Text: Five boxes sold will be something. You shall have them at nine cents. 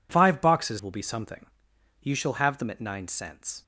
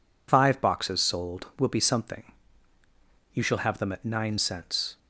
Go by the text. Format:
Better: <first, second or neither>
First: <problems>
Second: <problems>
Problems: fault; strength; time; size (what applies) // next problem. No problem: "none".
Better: second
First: skips "sold"; at 0.8 s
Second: none